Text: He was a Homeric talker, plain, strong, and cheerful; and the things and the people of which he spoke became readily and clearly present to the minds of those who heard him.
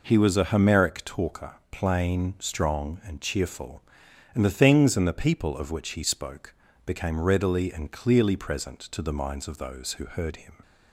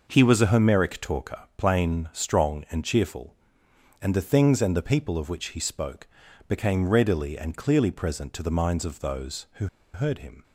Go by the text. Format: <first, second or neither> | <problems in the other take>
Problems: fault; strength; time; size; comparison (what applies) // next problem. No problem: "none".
first | pauses between "spoke" and "became"; at 6.0 s; 0.42 s long; slight in the first // pauses between "who" and "heard"; slight; at 9.6 s; 0.27 s long